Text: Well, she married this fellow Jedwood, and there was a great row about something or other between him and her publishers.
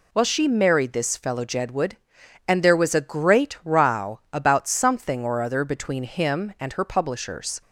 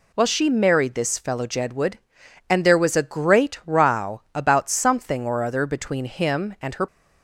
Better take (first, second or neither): first